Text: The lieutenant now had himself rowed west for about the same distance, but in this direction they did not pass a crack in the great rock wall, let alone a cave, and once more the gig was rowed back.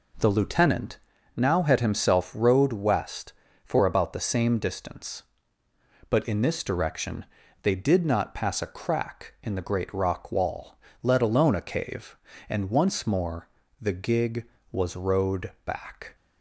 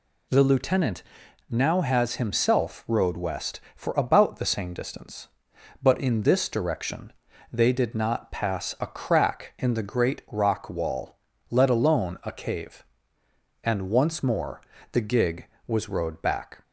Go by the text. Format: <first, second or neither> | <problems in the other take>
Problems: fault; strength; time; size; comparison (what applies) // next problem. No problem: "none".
first | pauses between "lieutenant" and "now"; noticeable; at 1.0 s; 0.46 s long; slight in the first // says "has" for "had"; at 1.8 s // pauses between "direction" and "they"; slight; at 7.1 s; 0.36 s long; also in the first // pauses between "more" and "the"; slight; at 14.6 s; 0.32 s long; slight in the first